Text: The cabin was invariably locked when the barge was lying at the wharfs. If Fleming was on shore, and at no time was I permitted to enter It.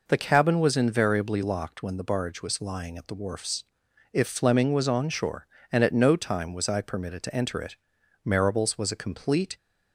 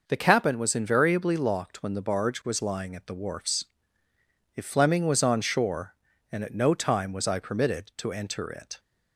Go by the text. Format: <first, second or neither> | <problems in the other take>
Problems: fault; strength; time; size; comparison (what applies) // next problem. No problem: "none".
second | goes on to say "Marables was a complete"; from 8.2 s on; 1.3 s long